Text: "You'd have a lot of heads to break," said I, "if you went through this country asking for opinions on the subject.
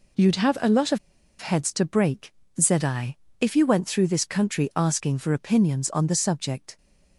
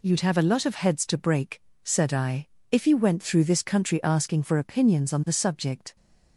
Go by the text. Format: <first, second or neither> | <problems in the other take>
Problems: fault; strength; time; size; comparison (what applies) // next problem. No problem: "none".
second | pauses between "of" and "heads"; at 0.9 s; 0.42 s long